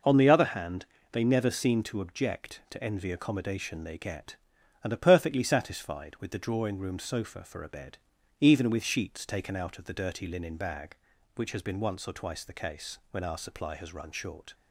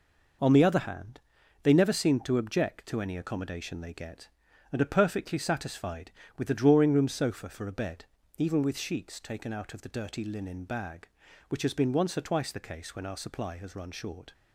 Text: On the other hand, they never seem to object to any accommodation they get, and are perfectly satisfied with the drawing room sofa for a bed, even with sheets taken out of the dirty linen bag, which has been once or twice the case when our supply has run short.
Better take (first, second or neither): second